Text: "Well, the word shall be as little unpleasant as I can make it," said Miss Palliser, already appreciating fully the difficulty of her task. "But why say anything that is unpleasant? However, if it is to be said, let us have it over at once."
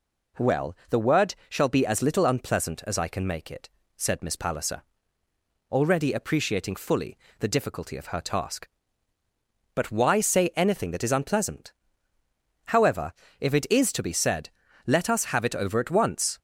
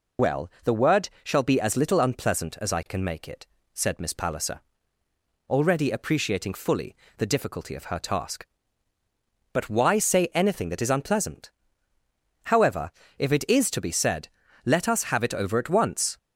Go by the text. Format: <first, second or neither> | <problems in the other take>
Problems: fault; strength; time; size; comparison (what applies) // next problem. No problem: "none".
first | loses the start of "Well"; at 0.1 s; 90 ms // pauses between "fully" and "the"; slight; at 6.9 s; 0.20 s long; slight in the first